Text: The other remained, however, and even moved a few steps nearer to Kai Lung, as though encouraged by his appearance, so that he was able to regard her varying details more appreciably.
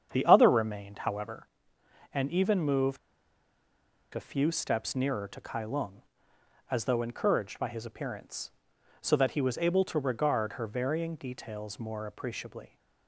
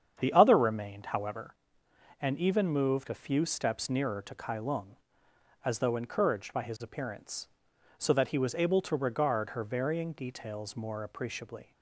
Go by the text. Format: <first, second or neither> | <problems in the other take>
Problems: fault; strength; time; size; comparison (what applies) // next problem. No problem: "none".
second | starts louder than the rest; strong; until 1.1 s; 8 dB; strong in the second // pauses between "moved" and "a"; at 2.9 s; 1.1 s long